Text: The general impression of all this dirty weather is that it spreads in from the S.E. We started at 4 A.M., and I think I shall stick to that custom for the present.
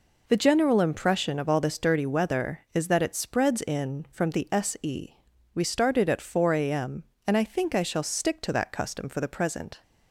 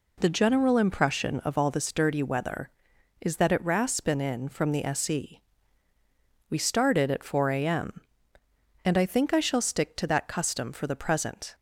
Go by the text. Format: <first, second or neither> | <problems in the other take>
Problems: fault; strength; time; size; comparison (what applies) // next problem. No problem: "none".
first | says "raspin" for "spreads"; at 3.6 s